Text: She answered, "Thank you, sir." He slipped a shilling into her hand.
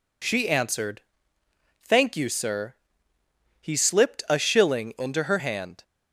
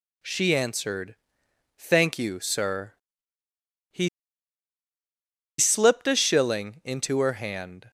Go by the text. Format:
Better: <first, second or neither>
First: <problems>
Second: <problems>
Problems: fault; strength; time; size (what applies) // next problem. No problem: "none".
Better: first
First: none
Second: pauses between "He" and "slipped"; strong; at 4.0 s; 1.5 s long